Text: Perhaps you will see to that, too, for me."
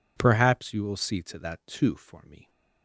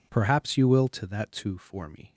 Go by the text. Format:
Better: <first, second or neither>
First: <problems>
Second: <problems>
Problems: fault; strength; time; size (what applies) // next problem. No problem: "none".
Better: first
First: none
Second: skips "see"; at 0.8 s